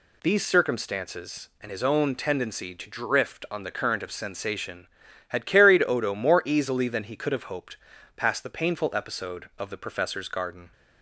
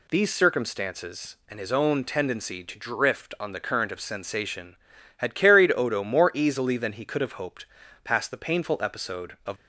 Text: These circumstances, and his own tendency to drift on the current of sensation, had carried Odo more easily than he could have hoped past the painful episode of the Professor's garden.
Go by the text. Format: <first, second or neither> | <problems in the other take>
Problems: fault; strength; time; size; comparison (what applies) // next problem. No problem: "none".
first | pauses between "hoped" and "past"; at 7.6 s; 0.38 s long; also in the first // stops before "the Professor's garden"; at 9.5 s